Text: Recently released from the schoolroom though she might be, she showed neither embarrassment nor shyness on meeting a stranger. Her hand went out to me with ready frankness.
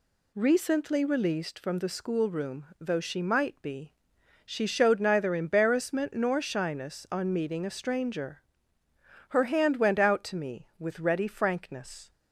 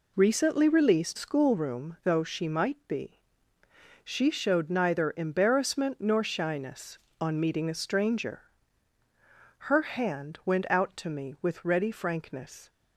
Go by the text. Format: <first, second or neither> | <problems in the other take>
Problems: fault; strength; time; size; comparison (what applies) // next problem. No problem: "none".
first | skips "from the"; at 1.1 s